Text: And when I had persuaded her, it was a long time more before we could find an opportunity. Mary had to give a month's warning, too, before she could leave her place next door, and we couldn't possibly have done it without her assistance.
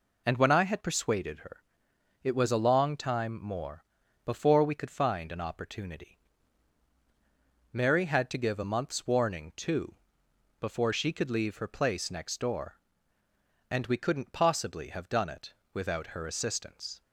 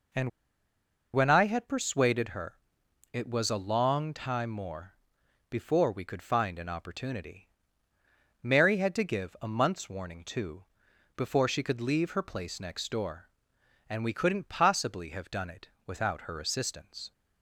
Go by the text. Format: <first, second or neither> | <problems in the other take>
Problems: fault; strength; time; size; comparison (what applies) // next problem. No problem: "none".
first | pauses between "And" and "when"; noticeable; at 0.2 s; 0.83 s long // pauses between "more" and "before"; noticeable; at 4.9 s; 0.56 s long; also in the first // pauses between "it" and "without"; slight; at 15.6 s; 0.18 s long; slight in the first